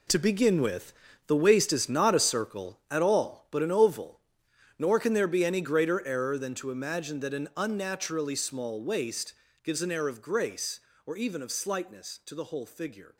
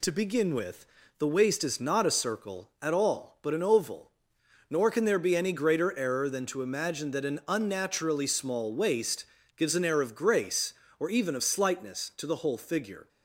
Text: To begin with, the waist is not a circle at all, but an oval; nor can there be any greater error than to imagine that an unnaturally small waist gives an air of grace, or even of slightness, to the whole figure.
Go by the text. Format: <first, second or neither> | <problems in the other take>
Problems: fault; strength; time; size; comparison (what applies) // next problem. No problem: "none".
second | gets quieter; strong; throughout; 11 dB // pauses between "waist" and "gives"; slight; at 9.3 s; 0.30 s long; slight in the second